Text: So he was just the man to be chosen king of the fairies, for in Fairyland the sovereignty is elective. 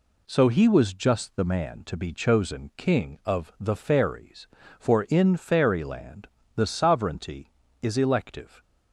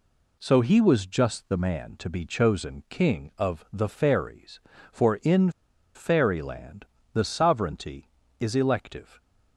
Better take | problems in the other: first | pauses between "in" and "Fairyland"; at 5.4 s; 0.45 s long // pauses between "Fairyland" and "the"; slight; at 6.8 s; 0.30 s long; slight in the first

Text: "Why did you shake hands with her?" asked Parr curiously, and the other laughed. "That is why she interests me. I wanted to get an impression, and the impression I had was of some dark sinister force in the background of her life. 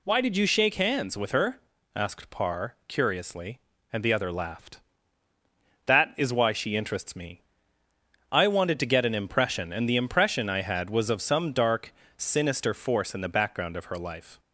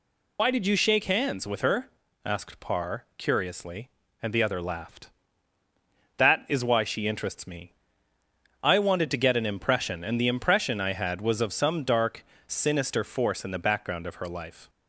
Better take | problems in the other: first | loses the start of "Why"; at 0.3 s; 50 ms // pauses between "dark" and "sinister"; slight; at 12.2 s; 0.23 s long; slight in the first

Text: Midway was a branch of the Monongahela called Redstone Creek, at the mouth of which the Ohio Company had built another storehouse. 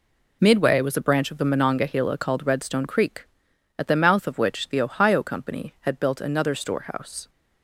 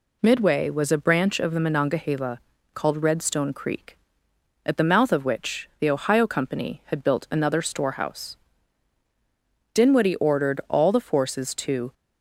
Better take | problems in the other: first | pauses between "Monongahela" and "called"; slight; at 2.4 s; 0.32 s long // goes on to say "Dinwiddie ordered all the forces to"; strong; from 9.7 s on; 2.2 s long

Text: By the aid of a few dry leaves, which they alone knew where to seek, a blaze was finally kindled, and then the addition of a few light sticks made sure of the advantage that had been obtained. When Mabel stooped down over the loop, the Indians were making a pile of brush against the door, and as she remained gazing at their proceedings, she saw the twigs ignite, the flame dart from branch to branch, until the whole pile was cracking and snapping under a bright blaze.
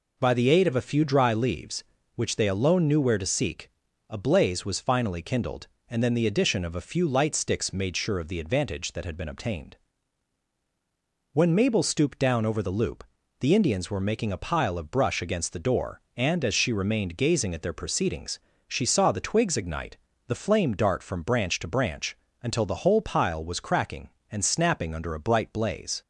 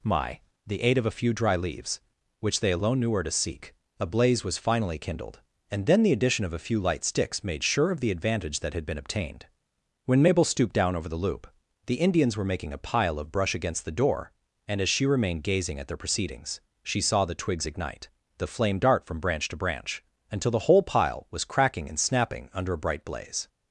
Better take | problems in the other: first | says "My" for "By"; at 0.0 s

